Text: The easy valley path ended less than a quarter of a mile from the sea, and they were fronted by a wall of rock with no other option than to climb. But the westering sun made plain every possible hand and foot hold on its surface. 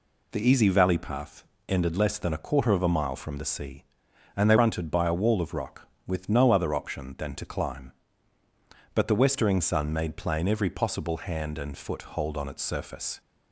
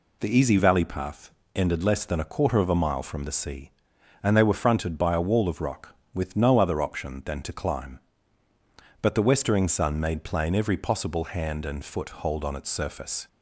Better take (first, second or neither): second